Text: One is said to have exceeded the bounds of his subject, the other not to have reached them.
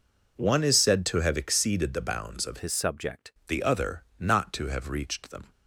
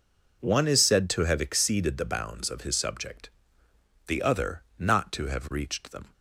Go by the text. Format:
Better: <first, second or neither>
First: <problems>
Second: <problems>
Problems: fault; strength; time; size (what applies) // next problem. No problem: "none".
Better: second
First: changes voice from "his" to "subject"; from 2.5 to 3.3 s; 0.8 s long // pauses between "other" and "not"; slight; at 4.0 s; 0.16 s long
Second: pauses between "other" and "not"; slight; at 4.6 s; 0.16 s long